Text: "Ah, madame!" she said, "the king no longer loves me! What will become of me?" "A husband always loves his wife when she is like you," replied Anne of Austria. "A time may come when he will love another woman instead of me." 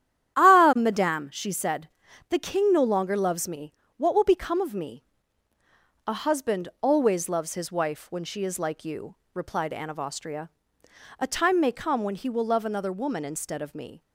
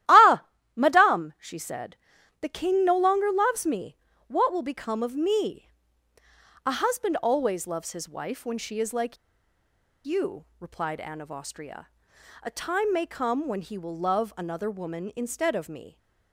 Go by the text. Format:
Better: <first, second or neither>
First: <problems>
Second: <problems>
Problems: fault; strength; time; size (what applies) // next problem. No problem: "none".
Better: first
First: starts louder than the rest; strong; until 1.4 s; 11 dB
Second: starts louder than the rest; strong; until 1.4 s; 13.5 dB // pauses between "like" and "you"; noticeable; at 9.1 s; 0.89 s long